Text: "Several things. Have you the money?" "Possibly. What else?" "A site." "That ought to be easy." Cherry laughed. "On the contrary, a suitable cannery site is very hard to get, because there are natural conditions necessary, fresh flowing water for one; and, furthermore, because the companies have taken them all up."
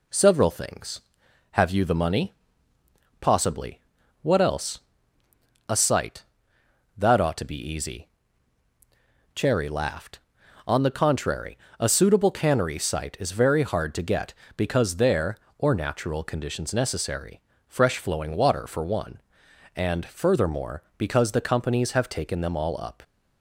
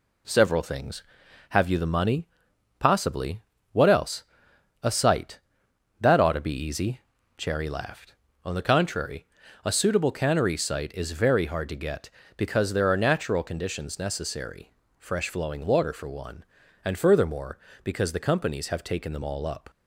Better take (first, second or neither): second